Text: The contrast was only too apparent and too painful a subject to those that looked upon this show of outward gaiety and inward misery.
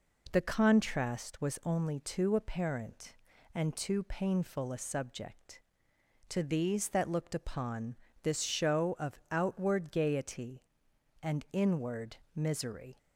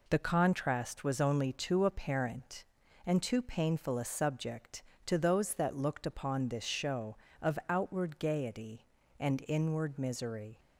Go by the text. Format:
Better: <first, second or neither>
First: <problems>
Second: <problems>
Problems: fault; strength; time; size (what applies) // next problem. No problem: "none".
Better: second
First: says "these" for "those"; at 6.4 s // pauses between "upon" and "this"; slight; at 7.9 s; 0.28 s long // pauses between "inward" and "misery"; slight; at 12.1 s; 0.18 s long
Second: none